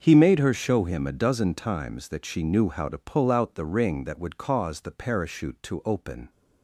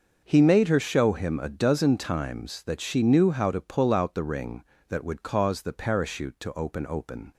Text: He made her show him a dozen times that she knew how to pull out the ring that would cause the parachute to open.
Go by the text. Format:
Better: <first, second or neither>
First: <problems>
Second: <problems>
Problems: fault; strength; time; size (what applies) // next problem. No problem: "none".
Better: first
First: starts louder than the rest; until 1.0 s; 6.5 dB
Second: starts louder than the rest; until 1.2 s; 6.5 dB // says "open" twice; at 6.8 s